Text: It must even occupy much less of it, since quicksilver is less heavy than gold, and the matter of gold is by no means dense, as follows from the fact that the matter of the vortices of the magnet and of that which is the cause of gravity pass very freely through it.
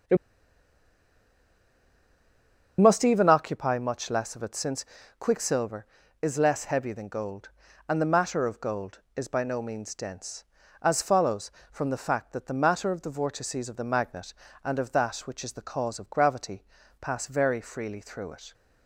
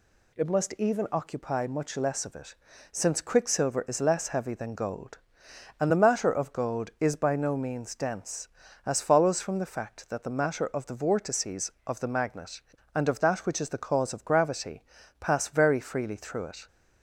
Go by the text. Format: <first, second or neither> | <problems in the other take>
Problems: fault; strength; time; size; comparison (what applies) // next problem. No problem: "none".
second | starts louder than the rest; strong; until 3.7 s; 7.5 dB // pauses between "It" and "must"; strong; at 0.1 s; 2.6 s long // pauses between "since" and "quicksilver"; at 4.8 s; 0.38 s long // pauses between "gravity" and "pass"; slight; at 16.6 s; 0.34 s long; slight in the second